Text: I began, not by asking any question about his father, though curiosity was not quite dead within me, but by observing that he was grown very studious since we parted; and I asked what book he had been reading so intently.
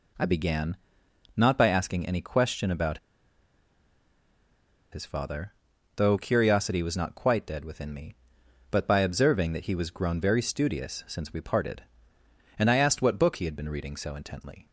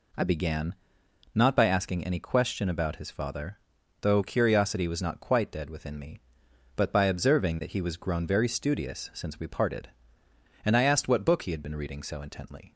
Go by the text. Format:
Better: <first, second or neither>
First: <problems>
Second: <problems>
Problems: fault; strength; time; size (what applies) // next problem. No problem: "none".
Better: second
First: pauses between "about" and "his"; strong; at 2.9 s; 1.9 s long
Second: none